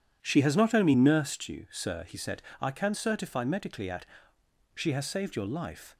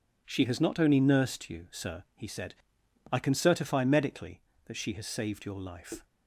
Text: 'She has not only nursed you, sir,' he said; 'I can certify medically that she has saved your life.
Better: second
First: says "at" for "that"; at 3.8 s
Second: none

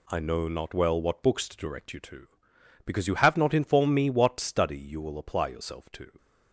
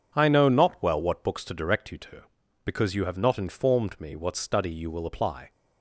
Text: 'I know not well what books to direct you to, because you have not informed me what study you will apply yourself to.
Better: first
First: none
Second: stops before "yourself to"; at 5.5 s

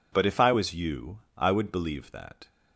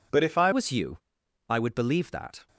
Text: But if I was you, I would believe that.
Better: first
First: none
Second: changes voice at "was"; from 0.5 s on; 1.9 s long

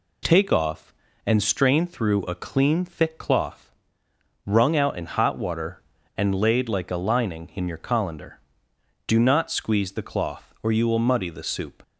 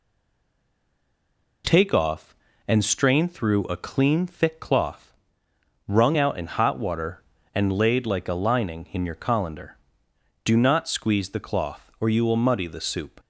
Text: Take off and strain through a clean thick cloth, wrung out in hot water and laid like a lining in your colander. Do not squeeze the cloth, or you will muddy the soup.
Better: first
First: none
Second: stays silent before the first word; noticeable; until 1.6 s; 1.6 s long

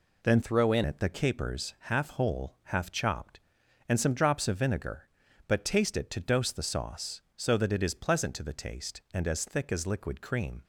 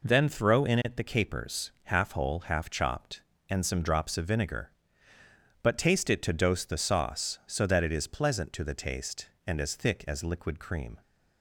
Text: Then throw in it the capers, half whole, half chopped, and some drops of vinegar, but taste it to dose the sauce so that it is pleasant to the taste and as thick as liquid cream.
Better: second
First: changes voice from "throw" to "in"; from 0.4 to 0.8 s; 0.4 s long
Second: none

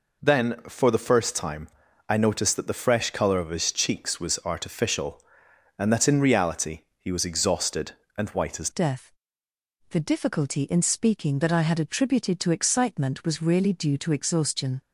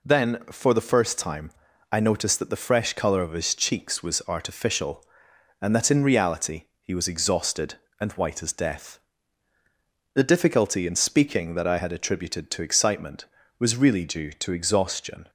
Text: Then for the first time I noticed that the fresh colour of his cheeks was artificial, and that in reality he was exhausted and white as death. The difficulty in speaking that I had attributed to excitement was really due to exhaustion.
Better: second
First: pauses between "time" and "I"; at 1.6 s; 0.40 s long // pauses between "reality" and "he"; slight; at 6.8 s; 0.18 s long // changes voice at "death"; from 8.7 s on; 6.1 s long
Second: pauses between "time" and "I"; at 1.5 s; 0.40 s long // pauses between "reality" and "he"; slight; at 6.6 s; 0.18 s long

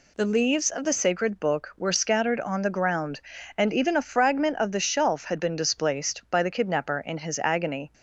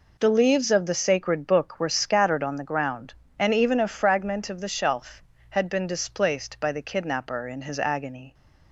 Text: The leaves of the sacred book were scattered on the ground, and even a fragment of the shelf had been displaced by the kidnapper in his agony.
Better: neither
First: none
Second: none

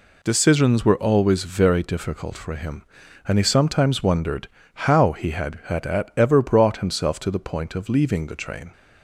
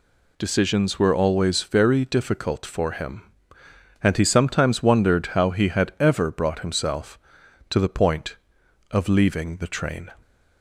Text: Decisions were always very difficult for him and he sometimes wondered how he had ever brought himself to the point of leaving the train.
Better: second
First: pauses between "wondered" and "how"; at 4.4 s; 0.40 s long // says "had" twice; at 5.6 s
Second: none

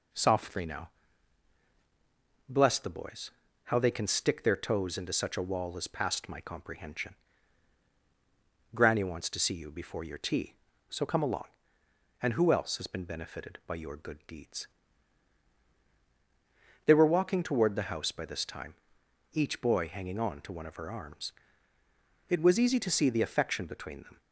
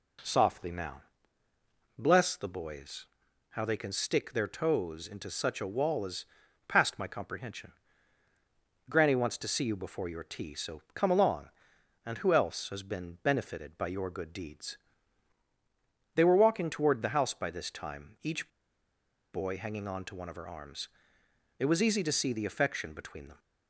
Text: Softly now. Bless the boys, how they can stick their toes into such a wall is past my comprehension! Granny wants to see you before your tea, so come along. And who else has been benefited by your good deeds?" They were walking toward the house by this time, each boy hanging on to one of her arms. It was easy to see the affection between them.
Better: first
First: none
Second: pauses between "is" and "past"; at 6.2 s; 0.42 s long // pauses between "each" and "boy"; noticeable; at 18.4 s; 0.83 s long

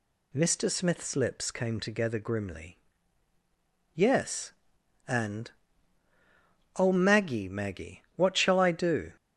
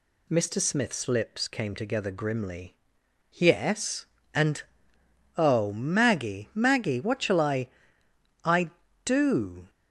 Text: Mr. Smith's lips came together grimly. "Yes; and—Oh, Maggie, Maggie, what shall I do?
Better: first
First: none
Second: says "I" twice; at 8.4 s

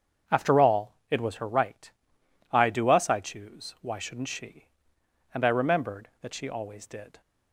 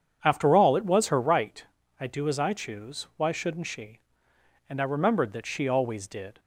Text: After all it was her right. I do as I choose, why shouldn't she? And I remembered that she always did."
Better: second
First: starts louder than the rest; strong; until 1.4 s; 7 dB // says "us" for "as"; at 2.8 s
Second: starts louder than the rest; strong; until 1.2 s; 8 dB

